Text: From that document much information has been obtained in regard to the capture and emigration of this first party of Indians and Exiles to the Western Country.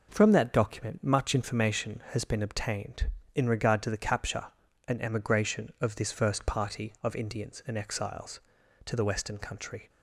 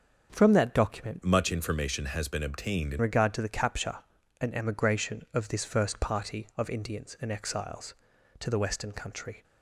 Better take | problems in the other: first | changes voice from "much" to "in"; from 1.2 to 2.9 s; 1.7 s long

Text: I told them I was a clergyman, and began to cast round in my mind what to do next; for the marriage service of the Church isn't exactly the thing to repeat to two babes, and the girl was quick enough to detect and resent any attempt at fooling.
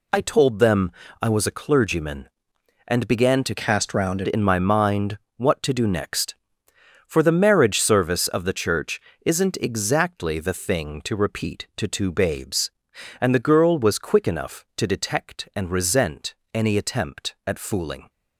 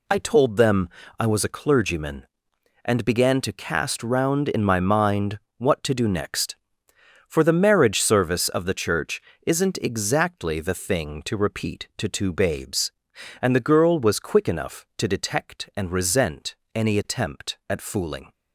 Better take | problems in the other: second | pauses between "them" and "I"; slight; at 0.9 s; 0.30 s long; slight in the second // changes voice from "cast" to "round"; from 3.5 to 4.2 s; 0.7 s long // pauses between "mind" and "what"; slight; at 5.1 s; 0.18 s long; slight in the second // pauses between "Church" and "isn't"; slight; at 8.9 s; 0.28 s long; slight in the second // pauses between "resent" and "any"; slight; at 16.3 s; 0.18 s long; slight in the second

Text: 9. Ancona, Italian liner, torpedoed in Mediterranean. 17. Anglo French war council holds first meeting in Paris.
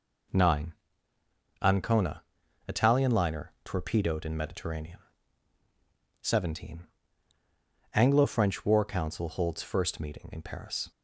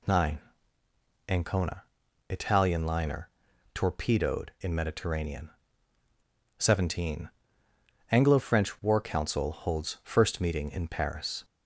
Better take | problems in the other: neither | none

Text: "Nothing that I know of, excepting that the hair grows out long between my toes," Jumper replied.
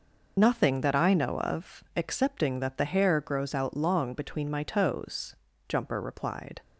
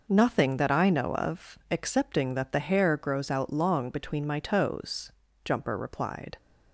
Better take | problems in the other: second | loses the start of "Nothing"; at 0.3 s; 45 ms

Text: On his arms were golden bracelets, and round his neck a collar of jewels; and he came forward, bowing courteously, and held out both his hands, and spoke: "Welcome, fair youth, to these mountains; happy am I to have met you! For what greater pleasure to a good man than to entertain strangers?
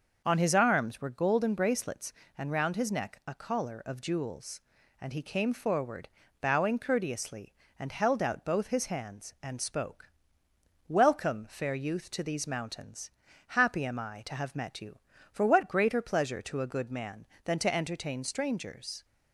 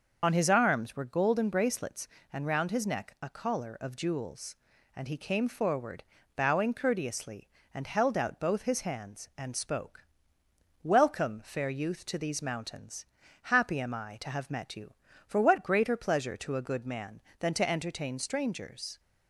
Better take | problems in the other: first | loses the start of "On"; at 0.2 s; 30 ms // starts louder than the rest; noticeable; until 1.2 s; 6 dB; noticeable in the first

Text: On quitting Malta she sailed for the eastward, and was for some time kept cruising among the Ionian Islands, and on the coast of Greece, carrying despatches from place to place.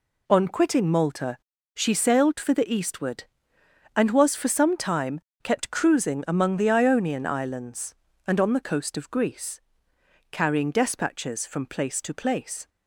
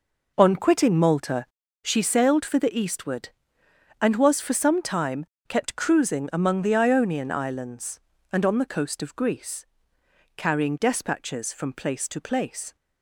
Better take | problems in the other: first | starts louder than the rest; noticeable; until 2.0 s; 5 dB // pauses between "Malta" and "she"; at 1.4 s; 0.38 s long; also in the first // pauses between "time" and "kept"; slight; at 5.2 s; 0.22 s long; slight in the first

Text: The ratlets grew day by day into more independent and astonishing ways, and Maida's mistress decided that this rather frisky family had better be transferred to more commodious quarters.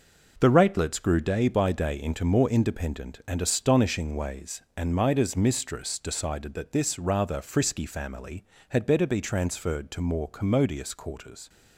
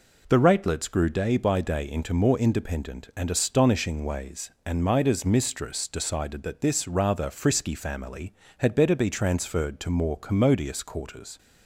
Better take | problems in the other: second | gets quieter; strong; throughout; 7.5 dB

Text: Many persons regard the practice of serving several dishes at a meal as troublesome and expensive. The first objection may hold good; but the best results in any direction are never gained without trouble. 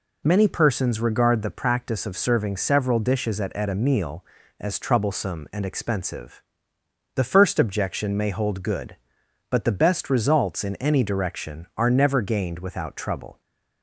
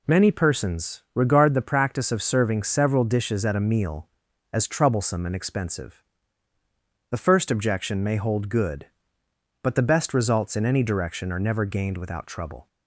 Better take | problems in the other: second | says "at" twice; at 3.5 s

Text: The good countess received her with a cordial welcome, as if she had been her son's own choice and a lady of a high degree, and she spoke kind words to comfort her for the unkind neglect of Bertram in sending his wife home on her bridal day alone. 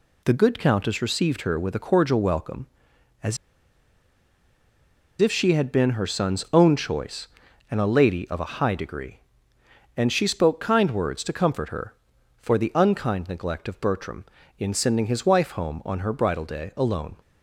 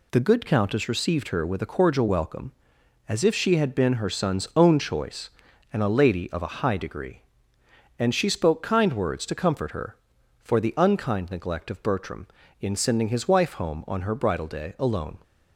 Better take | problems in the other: second | pauses between "as" and "if"; strong; at 3.3 s; 1.8 s long

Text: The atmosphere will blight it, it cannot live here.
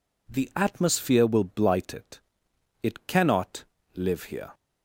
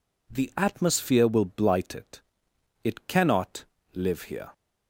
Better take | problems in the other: neither | pauses between "cannot" and "live"; slight; the same in both

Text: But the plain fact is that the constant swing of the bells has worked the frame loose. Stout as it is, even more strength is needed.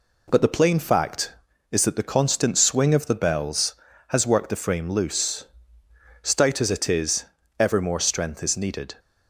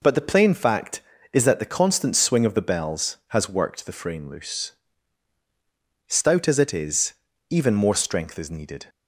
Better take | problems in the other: second | says "ever" for "even"; at 7.5 s

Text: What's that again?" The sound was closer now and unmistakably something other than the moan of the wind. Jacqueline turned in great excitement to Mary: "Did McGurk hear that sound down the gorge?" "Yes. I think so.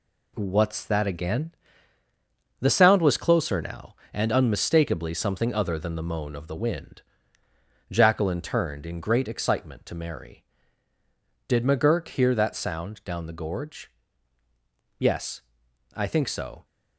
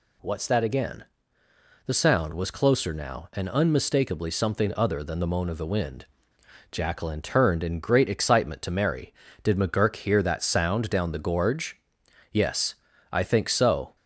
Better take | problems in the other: second | gets quieter; throughout; 6 dB

